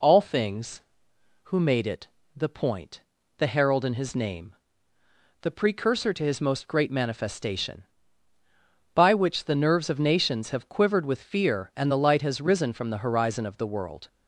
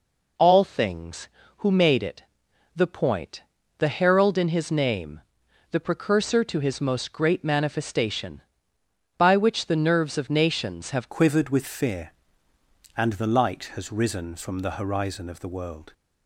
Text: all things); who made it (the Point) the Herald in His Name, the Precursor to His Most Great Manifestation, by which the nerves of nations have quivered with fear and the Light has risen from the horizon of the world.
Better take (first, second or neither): first